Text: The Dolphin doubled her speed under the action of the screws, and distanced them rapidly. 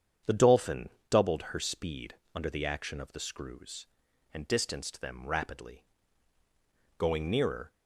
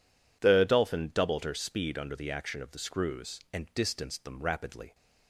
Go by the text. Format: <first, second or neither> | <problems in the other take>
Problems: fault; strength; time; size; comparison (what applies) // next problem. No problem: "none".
second | starts louder than the rest; strong; until 1.4 s; 8.5 dB // pauses between "Dolphin" and "doubled"; slight; at 0.8 s; 0.20 s long // pauses between "speed" and "under"; slight; at 2.1 s; 0.18 s long // goes on to say "Going nearer"; noticeable; from 6.9 s on; 0.76 s long